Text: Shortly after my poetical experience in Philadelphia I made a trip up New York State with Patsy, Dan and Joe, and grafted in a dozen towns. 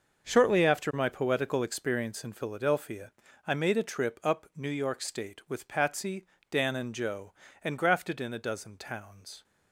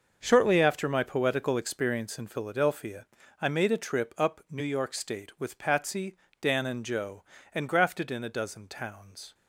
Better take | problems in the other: neither | starts louder than the rest; the same in both // pauses between "Philadelphia" and "I"; slight; the same in both

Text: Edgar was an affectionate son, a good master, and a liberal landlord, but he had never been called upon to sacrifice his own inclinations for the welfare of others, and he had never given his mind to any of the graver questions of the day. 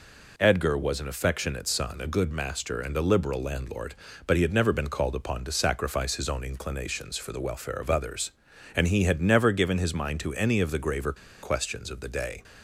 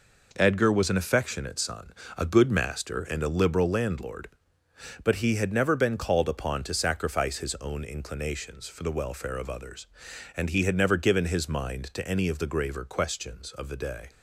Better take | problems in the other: second | pauses between "graver" and "questions"; slight; at 11.1 s; 0.28 s long

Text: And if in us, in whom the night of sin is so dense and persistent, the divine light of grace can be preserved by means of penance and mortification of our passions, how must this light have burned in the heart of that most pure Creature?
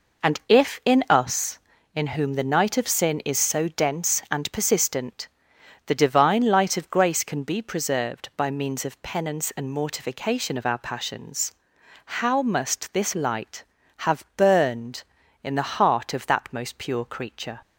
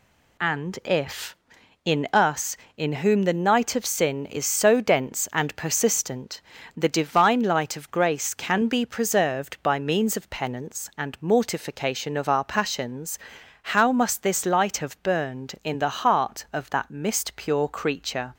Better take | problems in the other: first | says "mist" for "most"; at 16.8 s

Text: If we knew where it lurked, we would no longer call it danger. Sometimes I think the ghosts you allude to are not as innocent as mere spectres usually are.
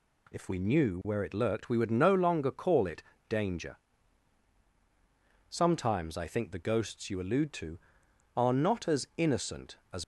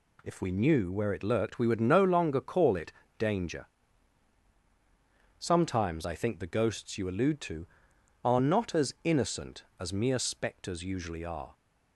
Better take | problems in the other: second | pauses between "it" and "danger"; slight; at 3.0 s; 0.26 s long; slight in the second // stops before "mere spectres usually are"; at 10.0 s

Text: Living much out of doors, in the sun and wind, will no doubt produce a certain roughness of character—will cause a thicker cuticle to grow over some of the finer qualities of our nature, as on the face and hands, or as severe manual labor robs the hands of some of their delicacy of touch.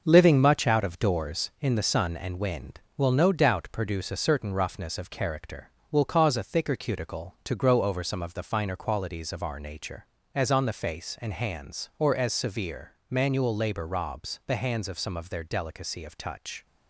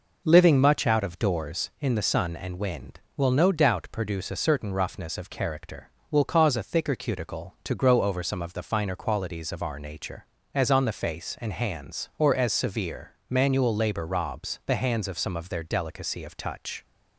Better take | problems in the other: second | gets quieter; throughout; 6.5 dB // pauses between "severe" and "manual"; slight; at 12.9 s; 0.18 s long; slight in the second

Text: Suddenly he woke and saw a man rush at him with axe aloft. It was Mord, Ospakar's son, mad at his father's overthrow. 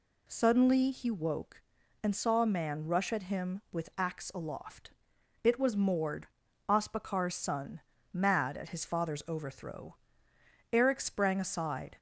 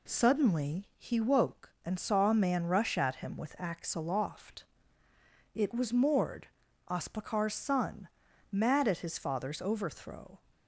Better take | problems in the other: second | goes on to say "Eric sprang aside"; noticeable; from 10.7 s on; 1.2 s long

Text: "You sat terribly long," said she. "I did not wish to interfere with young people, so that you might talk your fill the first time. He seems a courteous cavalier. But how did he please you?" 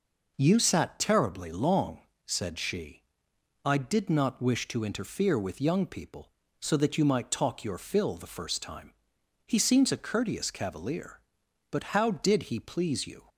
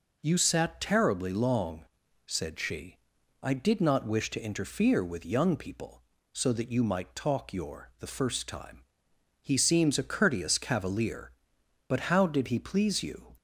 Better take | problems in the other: first | skips "fill"; at 7.9 s

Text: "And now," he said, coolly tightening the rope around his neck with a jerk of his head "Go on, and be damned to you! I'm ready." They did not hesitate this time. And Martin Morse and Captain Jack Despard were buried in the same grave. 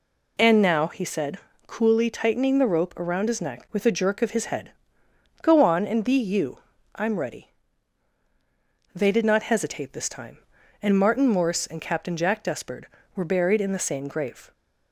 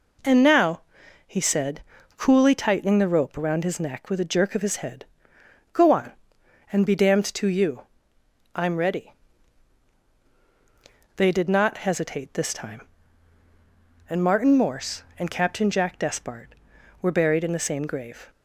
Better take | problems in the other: second | pauses between "head" and "Go"; noticeable; at 4.6 s; 0.72 s long; noticeable in the second // skips "damned to"; at 6.1 s

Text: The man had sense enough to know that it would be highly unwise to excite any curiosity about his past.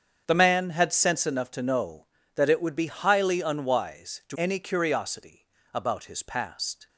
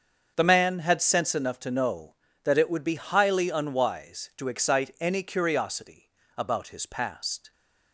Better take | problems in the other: second | starts louder than the rest; strong; until 1.2 s; 7.5 dB; also in the second // skips "excite"; at 4.3 s // pauses between "curiosity" and "about"; slight; at 5.4 s; 0.26 s long; slight in the second

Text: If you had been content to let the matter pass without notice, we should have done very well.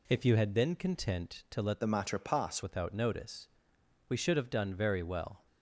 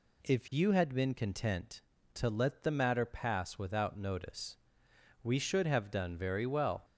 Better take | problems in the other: second | changes voice from "the" to "pass"; from 1.8 to 2.6 s; 0.8 s long

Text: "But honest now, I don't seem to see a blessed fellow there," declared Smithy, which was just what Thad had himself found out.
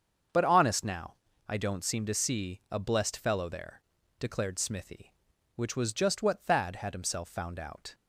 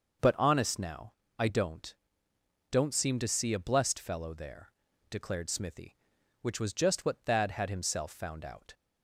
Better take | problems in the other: first | starts louder than the rest; until 1.4 s; 6 dB; also in the first // says "don't" twice; at 2.7 s

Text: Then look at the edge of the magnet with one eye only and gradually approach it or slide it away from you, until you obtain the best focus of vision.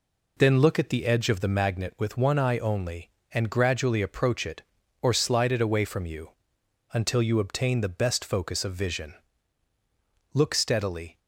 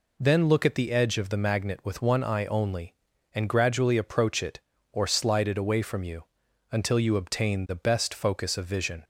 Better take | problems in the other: second | goes on to say "Look steadily"; noticeable; from 10.3 s on; 0.86 s long

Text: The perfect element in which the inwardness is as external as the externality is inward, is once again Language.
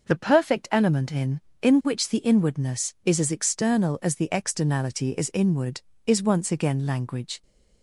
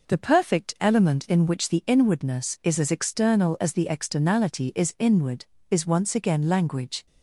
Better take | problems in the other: second | says "in" twice; at 1.6 s

